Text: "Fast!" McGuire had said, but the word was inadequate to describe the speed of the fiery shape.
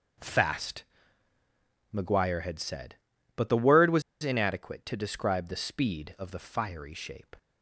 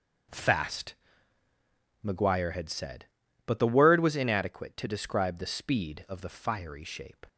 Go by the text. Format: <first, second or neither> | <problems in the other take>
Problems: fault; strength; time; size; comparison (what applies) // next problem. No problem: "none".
second | starts louder than the rest; until 2.3 s; 7 dB; also in the second // pauses between "was" and "inadequate"; slight; at 4.0 s; 0.21 s long